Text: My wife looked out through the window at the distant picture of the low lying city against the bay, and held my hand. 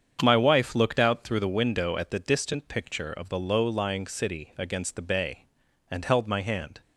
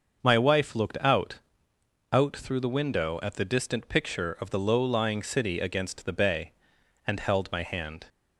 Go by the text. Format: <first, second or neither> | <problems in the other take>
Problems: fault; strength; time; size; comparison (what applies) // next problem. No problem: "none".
first | starts louder than the rest; until 1.2 s; 6.5 dB; strong in the first // says "out" twice; at 2.1 s